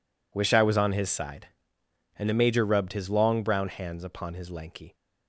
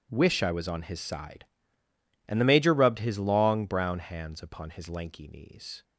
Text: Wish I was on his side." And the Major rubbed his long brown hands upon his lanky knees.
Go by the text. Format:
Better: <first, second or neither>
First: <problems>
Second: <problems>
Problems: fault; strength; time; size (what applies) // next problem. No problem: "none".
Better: second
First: stops before "knees"; at 4.9 s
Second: none